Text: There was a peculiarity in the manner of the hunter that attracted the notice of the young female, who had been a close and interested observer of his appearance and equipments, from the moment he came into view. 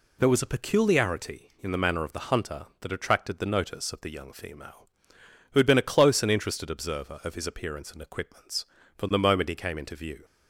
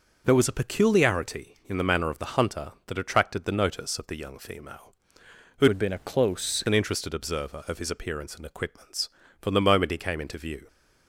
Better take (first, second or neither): first